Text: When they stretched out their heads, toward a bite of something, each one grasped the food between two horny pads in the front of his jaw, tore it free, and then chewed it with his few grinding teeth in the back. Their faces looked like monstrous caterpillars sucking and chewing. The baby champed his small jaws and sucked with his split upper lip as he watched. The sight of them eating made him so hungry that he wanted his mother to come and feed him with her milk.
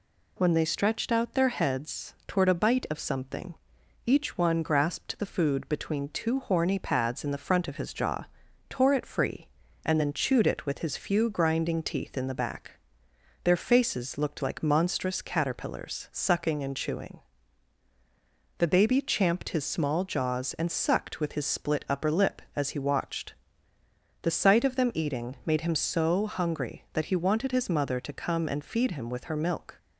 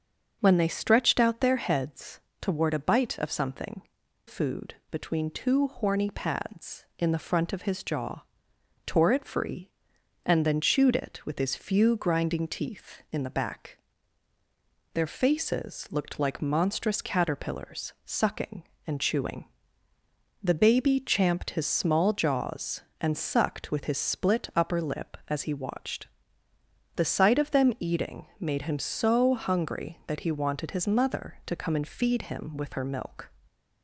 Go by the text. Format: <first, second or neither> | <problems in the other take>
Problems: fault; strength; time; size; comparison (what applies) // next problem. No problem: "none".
first | starts louder than the rest; until 1.4 s; 6.5 dB // skips "each one grasped the"; at 4.0 s // pauses between "eating" and "made"; slight; at 28.2 s; 0.16 s long